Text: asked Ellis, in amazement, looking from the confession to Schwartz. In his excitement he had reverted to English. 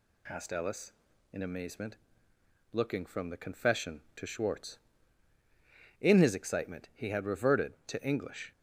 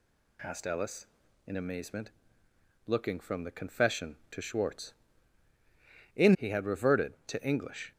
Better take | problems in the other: first | skips "his excitement"; at 6.3 s

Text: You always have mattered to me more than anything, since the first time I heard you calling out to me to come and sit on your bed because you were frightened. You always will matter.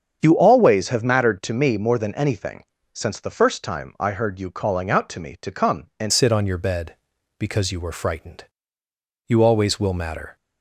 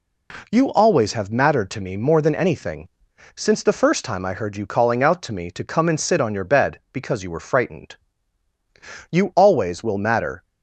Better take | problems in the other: second | starts louder than the rest; strong; until 1.2 s; 7.5 dB // changes voice at "sit"; from 6.1 s on; 4.2 s long

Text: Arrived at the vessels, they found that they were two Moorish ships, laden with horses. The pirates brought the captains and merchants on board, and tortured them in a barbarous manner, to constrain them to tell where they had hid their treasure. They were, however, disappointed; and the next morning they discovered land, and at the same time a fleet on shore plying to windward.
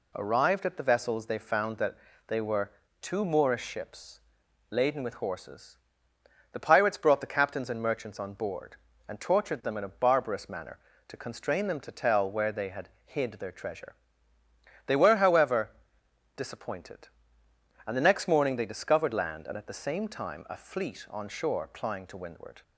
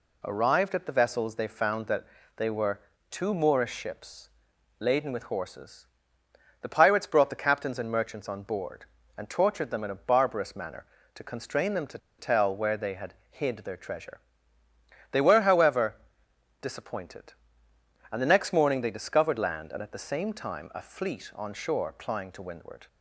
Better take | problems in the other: first | pauses between "that" and "they"; slight; at 2.0 s; 0.32 s long; slight in the first // pauses between "were" and "two"; slight; at 2.8 s; 0.30 s long; slight in the first // pauses between "to" and "tell"; slight; at 11.9 s; 0.21 s long // pauses between "had" and "hid"; slight; at 13.1 s; 0.16 s long; slight in the first

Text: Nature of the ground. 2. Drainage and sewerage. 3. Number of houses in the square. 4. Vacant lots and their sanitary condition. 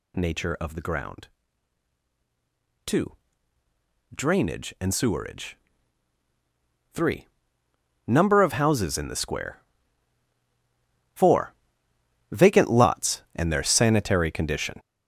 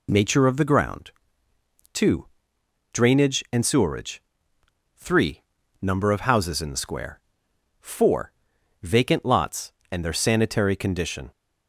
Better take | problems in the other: second | gets louder; strong; throughout; 7.5 dB

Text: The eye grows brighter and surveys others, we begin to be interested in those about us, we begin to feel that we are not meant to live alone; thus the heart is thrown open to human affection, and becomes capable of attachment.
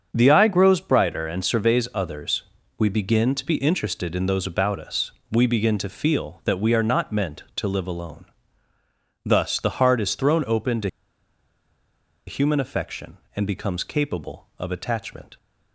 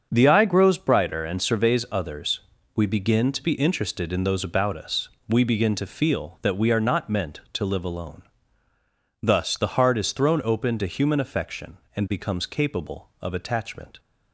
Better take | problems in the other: second | starts louder than the rest; until 1.1 s; 6.5 dB; also in the second // pauses between "to" and "human"; strong; at 10.8 s; 1.3 s long

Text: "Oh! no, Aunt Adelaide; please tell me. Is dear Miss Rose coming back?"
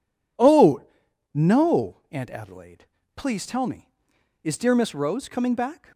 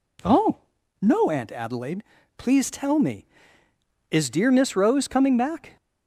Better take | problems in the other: neither | none

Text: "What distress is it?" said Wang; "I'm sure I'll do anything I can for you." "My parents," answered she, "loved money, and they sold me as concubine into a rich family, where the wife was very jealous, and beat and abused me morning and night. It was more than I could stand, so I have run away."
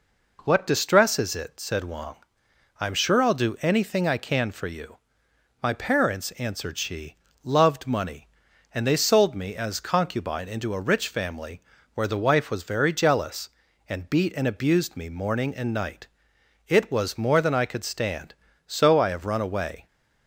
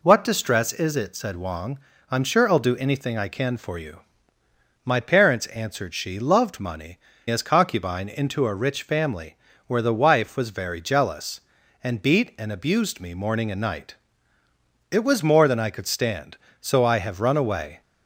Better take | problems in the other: first | skips "and they sold me"; at 7.1 s

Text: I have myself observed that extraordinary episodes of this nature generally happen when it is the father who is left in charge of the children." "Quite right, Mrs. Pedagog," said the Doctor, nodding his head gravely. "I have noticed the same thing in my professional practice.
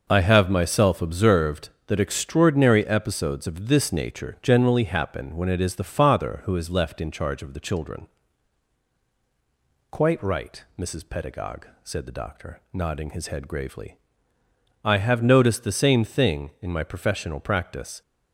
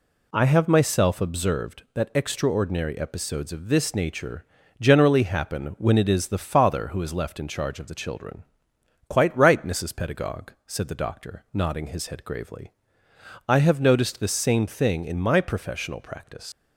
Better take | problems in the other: first | pauses between "nature" and "generally"; slight; at 4.4 s; 0.34 s long // leaves "practice" unfinished; at 16.5 s; 105 ms

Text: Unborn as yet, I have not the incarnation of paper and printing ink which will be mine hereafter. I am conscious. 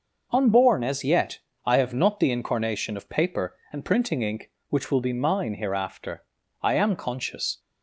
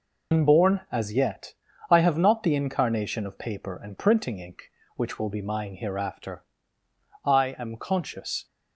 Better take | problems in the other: first | loses the start of "Unborn"; at 0.3 s; 105 ms

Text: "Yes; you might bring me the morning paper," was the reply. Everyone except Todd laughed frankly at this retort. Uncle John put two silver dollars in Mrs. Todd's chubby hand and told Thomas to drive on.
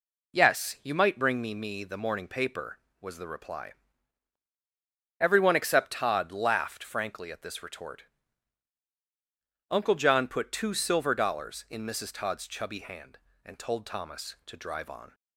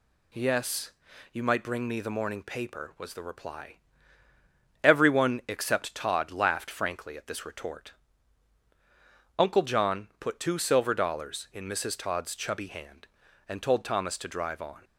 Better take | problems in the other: second | says "me" twice; at 1.5 s

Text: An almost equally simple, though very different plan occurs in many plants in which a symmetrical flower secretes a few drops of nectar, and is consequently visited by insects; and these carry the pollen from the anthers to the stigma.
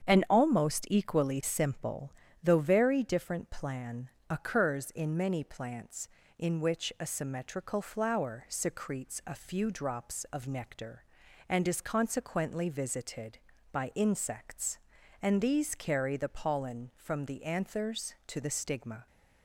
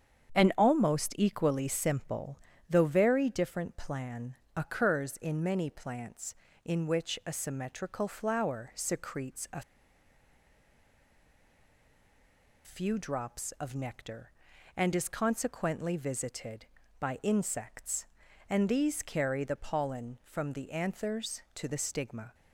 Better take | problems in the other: first | starts louder than the rest; strong; until 1.4 s; 8 dB; strong in the first // pauses between "plan" and "occurs"; slight; at 4.3 s; 0.18 s long; slight in the first // pauses between "a" and "few"; strong; at 9.6 s; 3.0 s long

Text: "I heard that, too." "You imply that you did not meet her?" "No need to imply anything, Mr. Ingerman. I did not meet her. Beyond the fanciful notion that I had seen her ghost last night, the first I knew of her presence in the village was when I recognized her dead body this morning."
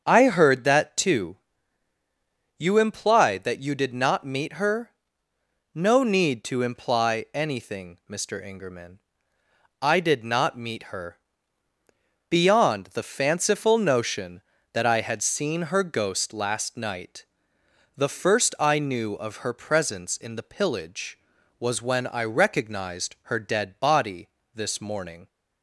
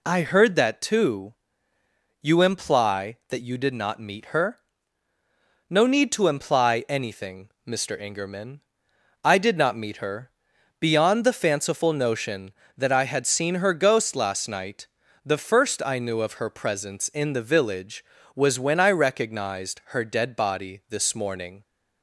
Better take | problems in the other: second | starts louder than the rest; until 1.0 s; 7 dB // says "pillage" for "village"; at 20.4 s // pauses between "body" and "this"; slight; at 24.2 s; 0.26 s long

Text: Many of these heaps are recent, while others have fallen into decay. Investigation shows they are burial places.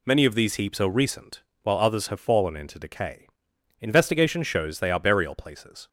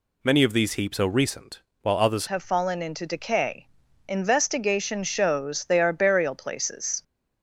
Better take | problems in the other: first | changes voice at "have"; from 2.2 s on; 4.8 s long

